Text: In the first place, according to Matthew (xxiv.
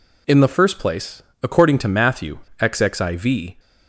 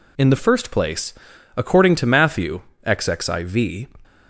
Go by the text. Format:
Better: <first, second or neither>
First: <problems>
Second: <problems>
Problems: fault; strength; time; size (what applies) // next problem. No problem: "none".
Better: neither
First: none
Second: none